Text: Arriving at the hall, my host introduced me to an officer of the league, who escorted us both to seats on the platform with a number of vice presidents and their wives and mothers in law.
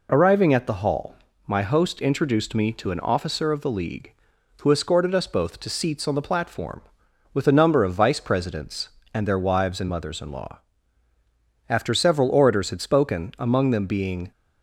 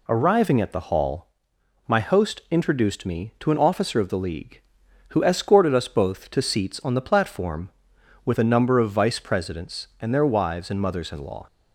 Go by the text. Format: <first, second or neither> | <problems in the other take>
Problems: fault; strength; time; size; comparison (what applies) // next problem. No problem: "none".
second | goes on to say "After several orators had spoken among them being"; strong; from 11.6 s on; 2.6 s long